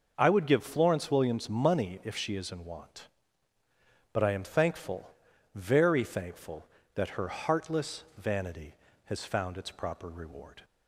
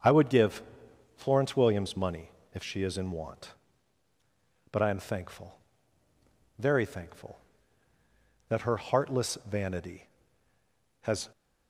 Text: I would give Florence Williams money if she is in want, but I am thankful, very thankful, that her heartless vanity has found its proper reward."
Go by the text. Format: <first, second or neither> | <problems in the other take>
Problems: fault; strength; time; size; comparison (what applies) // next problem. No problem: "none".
first | starts louder than the rest; until 1.5 s; 7 dB; noticeable in the first // pauses between "give" and "Florence"; noticeable; at 0.6 s; 0.54 s long // pauses between "money" and "if"; slight; at 2.3 s; 0.22 s long // stops before "found its proper reward"; at 11.3 s